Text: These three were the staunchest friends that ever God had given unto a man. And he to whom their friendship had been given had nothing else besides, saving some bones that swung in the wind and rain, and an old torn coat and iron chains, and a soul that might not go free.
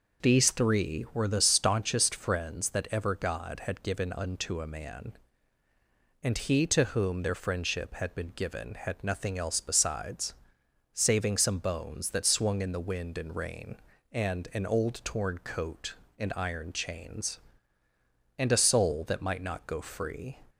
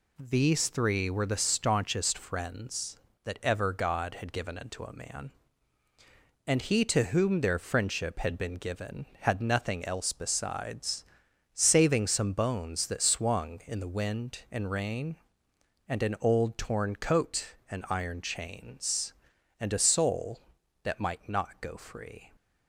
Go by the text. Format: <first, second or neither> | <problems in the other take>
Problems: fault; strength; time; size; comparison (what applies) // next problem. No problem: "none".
neither | none